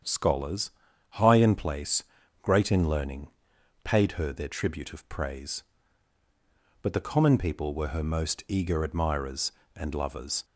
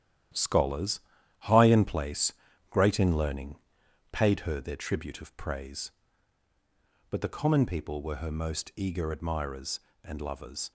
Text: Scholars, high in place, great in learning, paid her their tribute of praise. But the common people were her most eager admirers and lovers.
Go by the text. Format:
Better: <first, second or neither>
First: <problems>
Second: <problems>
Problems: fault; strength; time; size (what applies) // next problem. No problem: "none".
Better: first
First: starts louder than the rest; strong; until 1.4 s; 8 dB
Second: gets quieter; strong; throughout; 8 dB // starts louder than the rest; strong; until 1.7 s; 11 dB